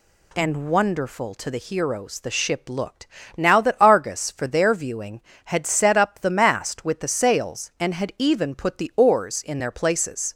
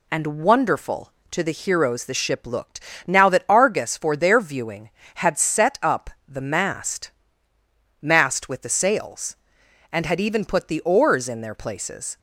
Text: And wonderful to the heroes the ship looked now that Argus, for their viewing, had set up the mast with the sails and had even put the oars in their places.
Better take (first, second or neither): first